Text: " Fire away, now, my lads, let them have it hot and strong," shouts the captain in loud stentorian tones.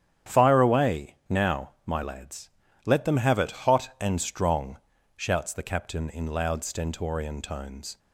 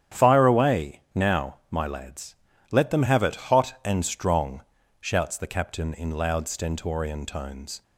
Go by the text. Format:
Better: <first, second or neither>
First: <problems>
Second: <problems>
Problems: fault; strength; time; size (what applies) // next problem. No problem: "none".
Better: neither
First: starts louder than the rest; strong; until 1.4 s; 9.5 dB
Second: starts louder than the rest; strong; until 1.2 s; 9.5 dB